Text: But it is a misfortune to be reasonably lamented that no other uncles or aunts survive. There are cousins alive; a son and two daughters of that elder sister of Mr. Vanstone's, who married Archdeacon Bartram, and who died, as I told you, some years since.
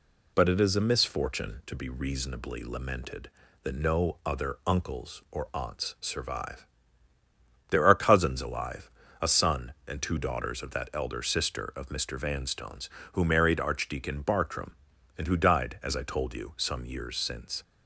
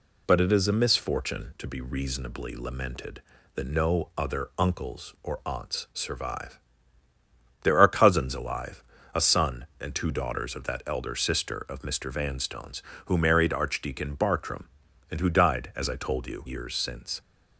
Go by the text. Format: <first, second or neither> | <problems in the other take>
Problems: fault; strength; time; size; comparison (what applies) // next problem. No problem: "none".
first | skips "some"; at 16.4 s